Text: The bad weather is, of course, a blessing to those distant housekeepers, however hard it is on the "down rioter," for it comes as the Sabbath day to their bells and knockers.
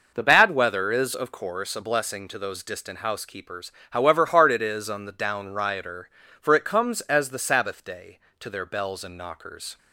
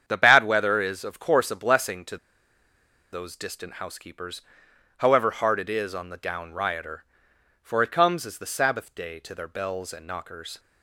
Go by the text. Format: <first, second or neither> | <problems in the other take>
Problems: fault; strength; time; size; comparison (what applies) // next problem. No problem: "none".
first | starts louder than the rest; strong; until 1.0 s; 8 dB // pauses between "to" and "those"; noticeable; at 2.1 s; 0.95 s long